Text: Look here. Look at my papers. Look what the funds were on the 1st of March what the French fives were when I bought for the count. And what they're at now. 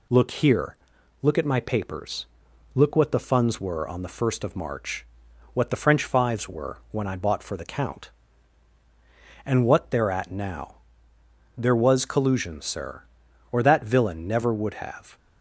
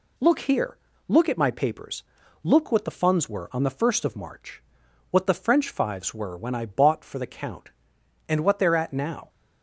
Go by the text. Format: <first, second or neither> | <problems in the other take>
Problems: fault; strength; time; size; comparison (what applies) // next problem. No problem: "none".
second | pauses between "March" and "what"; noticeable; at 5.0 s; 0.48 s long; noticeable in the second // goes on to say "There was collusion sir or that villain never would have"; strong; from 11.5 s on; 3.6 s long